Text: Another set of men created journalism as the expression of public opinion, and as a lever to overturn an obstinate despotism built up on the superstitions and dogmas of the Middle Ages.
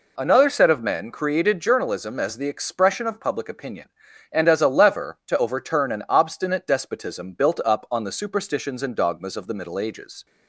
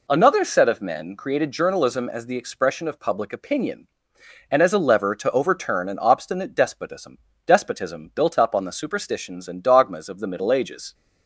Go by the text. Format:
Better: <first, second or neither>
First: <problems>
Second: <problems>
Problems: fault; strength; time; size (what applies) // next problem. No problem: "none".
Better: first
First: none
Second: says "despotism" twice; at 7.4 s